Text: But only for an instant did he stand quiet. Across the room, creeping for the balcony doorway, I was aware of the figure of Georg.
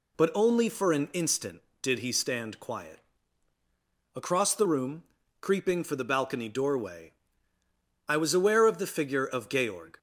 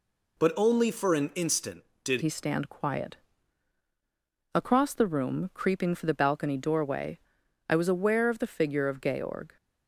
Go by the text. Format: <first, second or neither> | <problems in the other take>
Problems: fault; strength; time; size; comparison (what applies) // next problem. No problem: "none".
first | changes voice at "he"; from 2.2 s on; 7.3 s long